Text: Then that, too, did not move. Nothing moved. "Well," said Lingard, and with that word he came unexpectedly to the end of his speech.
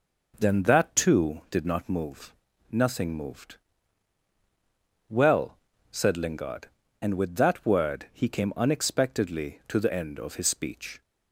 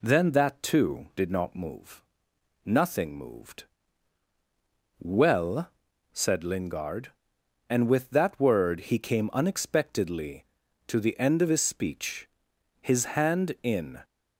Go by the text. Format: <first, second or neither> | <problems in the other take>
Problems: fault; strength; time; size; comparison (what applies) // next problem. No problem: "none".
first | goes on to say "His hand in"; noticeable; from 12.8 s on; 1.2 s long